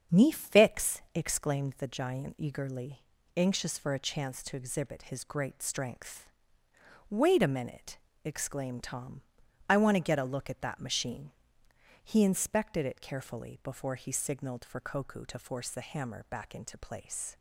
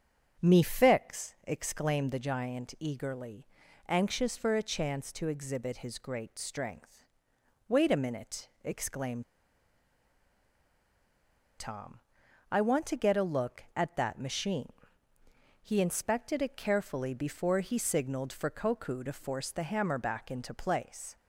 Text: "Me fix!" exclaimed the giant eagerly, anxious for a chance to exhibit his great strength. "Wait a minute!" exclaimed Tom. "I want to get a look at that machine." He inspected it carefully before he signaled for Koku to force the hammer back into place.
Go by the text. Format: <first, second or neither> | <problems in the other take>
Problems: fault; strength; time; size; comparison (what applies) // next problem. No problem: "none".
first | starts louder than the rest; strong; until 1.4 s; 7.5 dB; strong in the first // pauses between "exclaimed" and "Tom"; strong; at 9.2 s; 2.3 s long